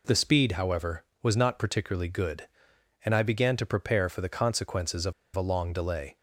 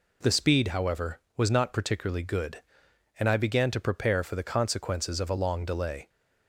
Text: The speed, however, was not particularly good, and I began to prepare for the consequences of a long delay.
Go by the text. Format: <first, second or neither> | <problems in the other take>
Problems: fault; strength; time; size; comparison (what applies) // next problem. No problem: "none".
second | pauses between "of" and "a"; slight; at 5.1 s; 0.23 s long